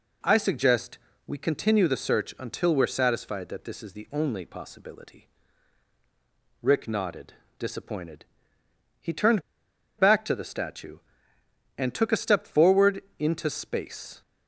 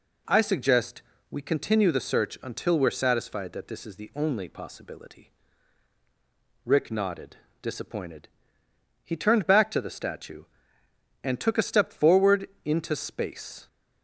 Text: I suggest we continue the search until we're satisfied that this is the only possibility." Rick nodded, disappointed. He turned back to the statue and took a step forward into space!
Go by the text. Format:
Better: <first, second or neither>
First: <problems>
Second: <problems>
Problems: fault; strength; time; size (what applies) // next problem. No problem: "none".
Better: second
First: pauses between "suggest" and "we"; slight; at 0.9 s; 0.26 s long // pauses between "turned" and "back"; noticeable; at 9.4 s; 0.57 s long // pauses between "forward" and "into"; slight; at 13.0 s; 0.16 s long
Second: pauses between "suggest" and "we"; slight; at 1.0 s; 0.26 s long // pauses between "forward" and "into"; slight; at 12.4 s; 0.16 s long